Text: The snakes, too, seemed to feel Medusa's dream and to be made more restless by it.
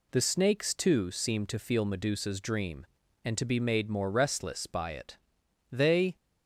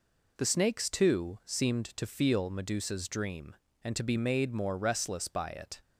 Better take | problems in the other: second | goes on to say "They"; slight; from 5.7 s on; 0.44 s long

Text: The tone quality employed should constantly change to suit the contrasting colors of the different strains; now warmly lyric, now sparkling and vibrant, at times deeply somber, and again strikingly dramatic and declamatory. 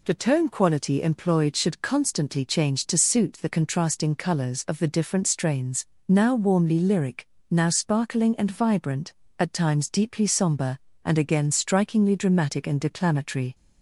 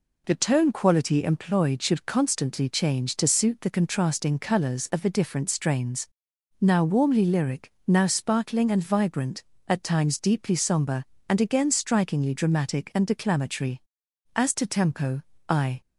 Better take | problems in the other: first | goes on to say "As to tempo I"; from 14.3 s on; 1.4 s long

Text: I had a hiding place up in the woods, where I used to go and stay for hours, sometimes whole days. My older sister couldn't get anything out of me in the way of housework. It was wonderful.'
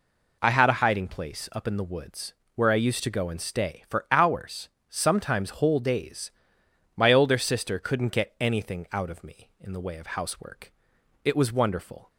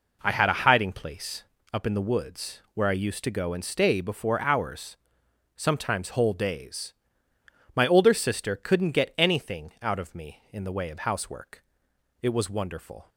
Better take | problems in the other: first | pauses between "place" and "up"; slight; at 1.4 s; 0.28 s long // says "before" for "for"; at 3.9 s

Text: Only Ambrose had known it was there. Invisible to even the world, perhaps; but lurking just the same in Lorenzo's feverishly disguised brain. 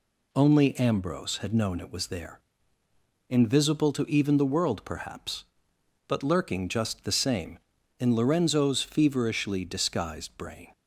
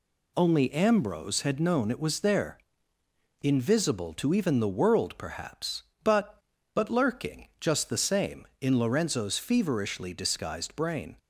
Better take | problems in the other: first | says "but" twice; at 6.7 s

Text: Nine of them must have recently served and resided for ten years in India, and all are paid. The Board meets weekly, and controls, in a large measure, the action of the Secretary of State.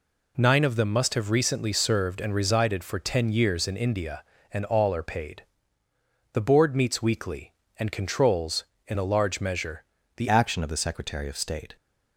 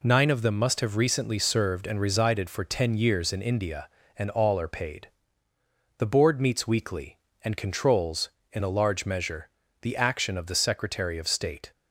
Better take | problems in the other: second | changes voice at "action"; from 10.2 s on; 1.5 s long

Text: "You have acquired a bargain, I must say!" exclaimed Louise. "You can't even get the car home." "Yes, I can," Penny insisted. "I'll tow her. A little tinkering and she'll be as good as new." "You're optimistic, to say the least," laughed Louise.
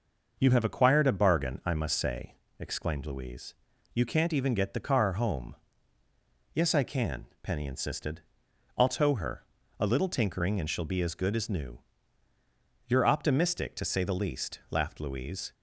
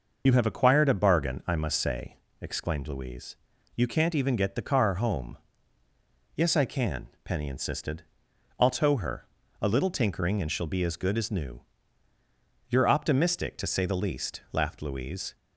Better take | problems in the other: first | loses the start of "You"; at 0.2 s; 45 ms

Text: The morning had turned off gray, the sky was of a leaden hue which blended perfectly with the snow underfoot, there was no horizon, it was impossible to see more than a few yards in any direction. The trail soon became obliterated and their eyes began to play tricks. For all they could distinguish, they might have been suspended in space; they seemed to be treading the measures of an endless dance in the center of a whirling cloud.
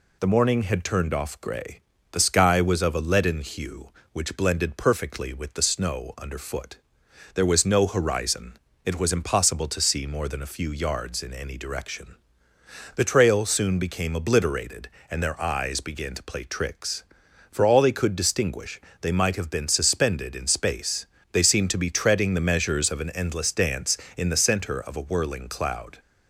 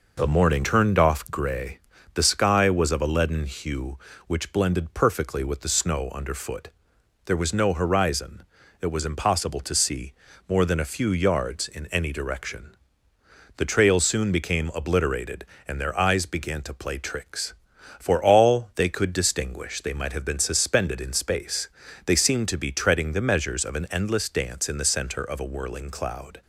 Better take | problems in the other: first | skips "had"; at 0.6 s // pauses between "see" and "more"; at 10.1 s; 0.38 s long

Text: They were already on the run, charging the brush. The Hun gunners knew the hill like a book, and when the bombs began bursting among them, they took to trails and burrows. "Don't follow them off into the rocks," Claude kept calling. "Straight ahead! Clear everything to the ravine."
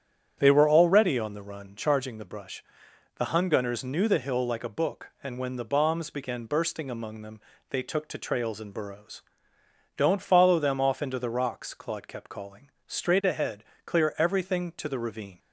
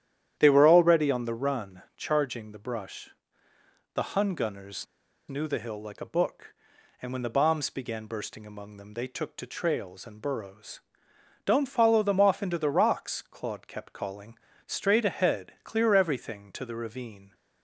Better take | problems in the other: first | starts louder than the rest; strong; until 1.3 s; 10.5 dB; strong in the first // pauses between "gunners" and "knew"; at 4.8 s; 0.43 s long

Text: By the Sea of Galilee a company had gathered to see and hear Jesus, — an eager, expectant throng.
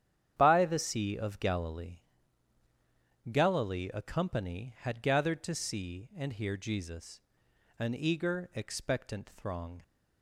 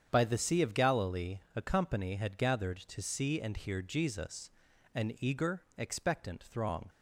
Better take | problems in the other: second | starts louder than the rest; strong; until 1.3 s; 9.5 dB; strong in the second // says "Galilee" twice; at 3.3 s

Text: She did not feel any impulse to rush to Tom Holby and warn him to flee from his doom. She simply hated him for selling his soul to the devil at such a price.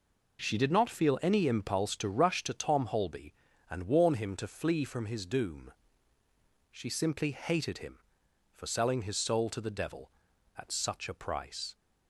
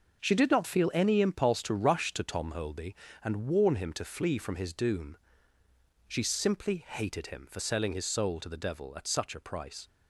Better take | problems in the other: neither | none

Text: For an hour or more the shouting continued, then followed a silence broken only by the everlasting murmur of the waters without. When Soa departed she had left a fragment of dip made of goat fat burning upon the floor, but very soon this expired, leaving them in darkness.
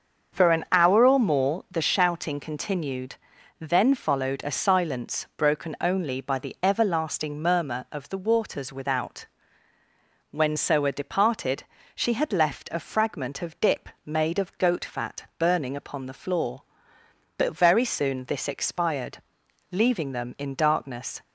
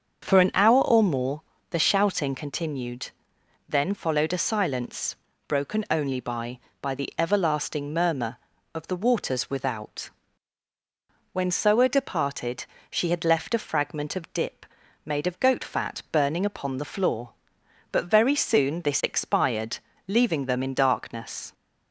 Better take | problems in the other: first | starts louder than the rest; until 1.2 s; 7 dB; also in the first // pauses between "more" and "the"; slight; at 1.4 s; 0.30 s long // pauses between "silence" and "broken"; slight; at 5.1 s; 0.32 s long // says "by" twice; at 6.7 s // pauses between "departed" and "she"; slight; at 12.6 s; 0.26 s long; slight in the first // pauses between "dip" and "made"; at 14.6 s; 0.38 s long; slight in the first

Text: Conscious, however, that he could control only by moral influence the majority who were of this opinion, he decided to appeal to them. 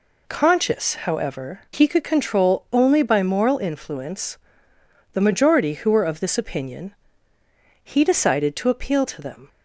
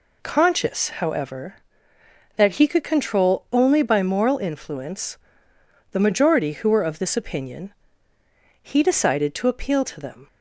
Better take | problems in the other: second | skips "that"; at 1.6 s // pauses between "influence" and "the"; noticeable; at 4.3 s; 0.78 s long; noticeable in the second

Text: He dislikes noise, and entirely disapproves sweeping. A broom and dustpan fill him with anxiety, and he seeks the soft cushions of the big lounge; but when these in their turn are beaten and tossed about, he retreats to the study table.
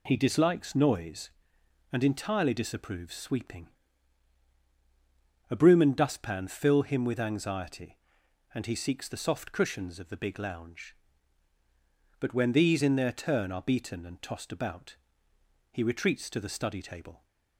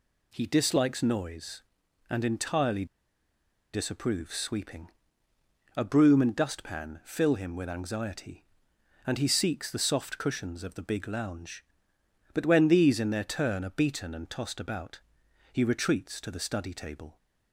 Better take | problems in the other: first | pauses between "entirely" and "disapproves"; noticeable; at 2.8 s; 0.87 s long

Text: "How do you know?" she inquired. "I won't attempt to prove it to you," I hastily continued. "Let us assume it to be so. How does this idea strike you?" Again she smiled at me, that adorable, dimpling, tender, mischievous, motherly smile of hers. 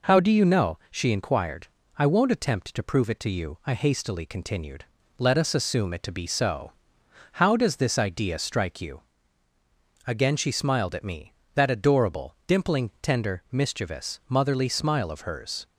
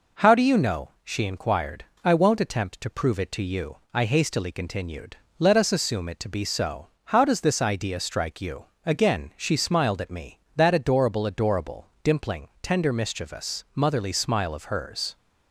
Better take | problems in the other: first | says "adorable" twice; at 11.2 s

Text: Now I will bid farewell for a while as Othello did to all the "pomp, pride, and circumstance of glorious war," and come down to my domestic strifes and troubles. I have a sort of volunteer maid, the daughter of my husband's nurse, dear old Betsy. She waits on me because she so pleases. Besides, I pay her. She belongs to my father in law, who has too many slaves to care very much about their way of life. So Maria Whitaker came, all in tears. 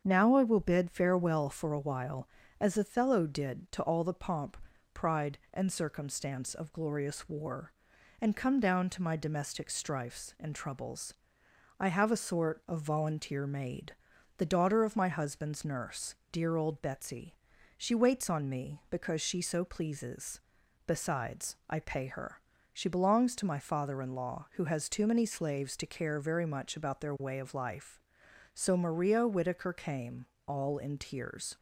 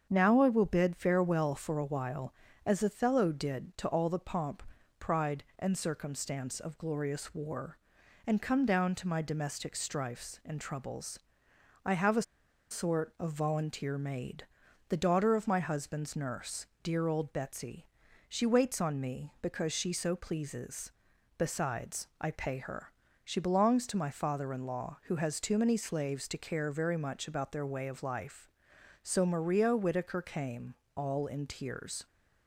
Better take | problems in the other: first | starts louder than the rest; strong; until 1.1 s; 7 dB; strong in the first // pauses between "a" and "sort"; noticeable; at 12.2 s; 0.48 s long

